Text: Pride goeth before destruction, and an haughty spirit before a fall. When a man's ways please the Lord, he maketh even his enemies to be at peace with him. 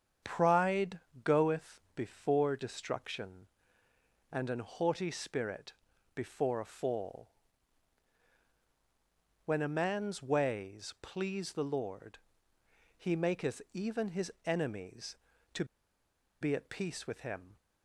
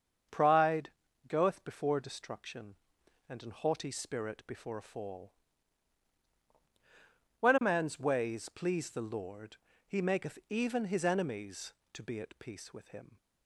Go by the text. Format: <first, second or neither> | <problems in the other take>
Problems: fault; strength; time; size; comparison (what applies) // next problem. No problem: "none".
second | starts louder than the rest; strong; until 1.5 s; 8 dB; also in the second // pauses between "Pride" and "goeth"; slight; at 0.9 s; 0.26 s long; slight in the second // pauses between "spirit" and "before"; at 5.7 s; 0.42 s long // pauses between "his" and "enemies"; slight; at 14.3 s; 0.16 s long // pauses between "to" and "be"; noticeable; at 15.6 s; 0.76 s long